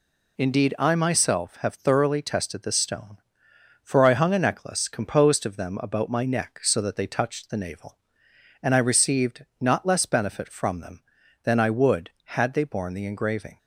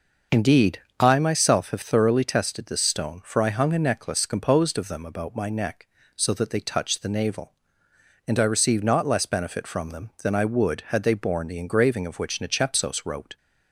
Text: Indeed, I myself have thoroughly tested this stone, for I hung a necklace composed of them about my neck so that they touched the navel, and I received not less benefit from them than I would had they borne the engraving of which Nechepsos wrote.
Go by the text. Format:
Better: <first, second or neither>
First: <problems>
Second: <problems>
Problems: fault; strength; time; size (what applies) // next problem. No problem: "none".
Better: second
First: stops before "of which Nechepsos wrote"; at 13.5 s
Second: none